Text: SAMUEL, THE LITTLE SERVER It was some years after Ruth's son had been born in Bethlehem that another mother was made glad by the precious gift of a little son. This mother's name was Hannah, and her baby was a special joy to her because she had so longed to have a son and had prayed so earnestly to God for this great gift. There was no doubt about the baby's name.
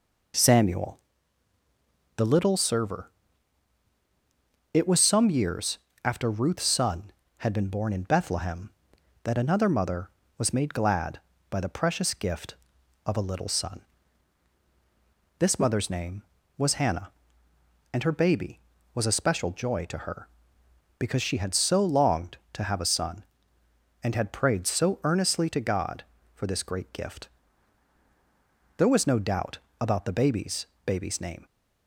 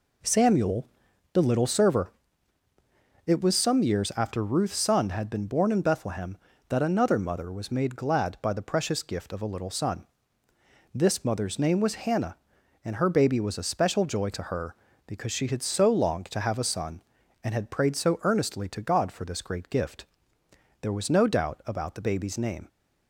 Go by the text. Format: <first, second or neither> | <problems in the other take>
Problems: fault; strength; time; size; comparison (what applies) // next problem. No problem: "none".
second | pauses between "SERVER" and "It"; strong; at 3.0 s; 1.6 s long; also in the second // pauses between "years" and "after"; slight; at 5.7 s; 0.26 s long // pauses between "doubt" and "about"; slight; at 29.5 s; 0.22 s long // says "baby's" twice; at 30.8 s